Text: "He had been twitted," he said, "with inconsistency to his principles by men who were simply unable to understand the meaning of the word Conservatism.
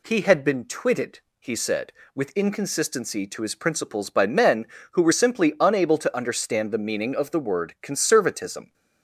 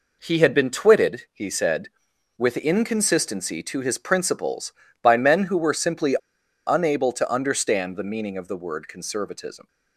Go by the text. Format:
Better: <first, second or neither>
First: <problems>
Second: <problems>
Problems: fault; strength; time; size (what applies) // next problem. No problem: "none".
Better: first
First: none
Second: pauses between "simply" and "unable"; noticeable; at 6.1 s; 0.49 s long